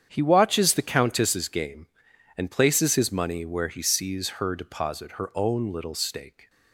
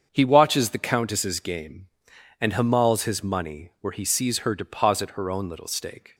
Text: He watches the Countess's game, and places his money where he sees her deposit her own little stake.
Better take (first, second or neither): first